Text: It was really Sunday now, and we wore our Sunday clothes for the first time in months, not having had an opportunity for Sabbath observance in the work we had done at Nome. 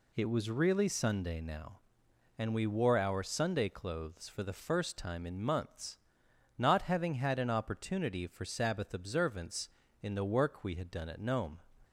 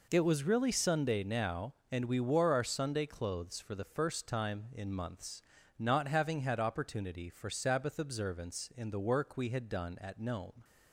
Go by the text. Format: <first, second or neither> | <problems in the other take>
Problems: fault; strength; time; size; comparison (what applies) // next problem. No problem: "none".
first | skips "an"; at 6.5 s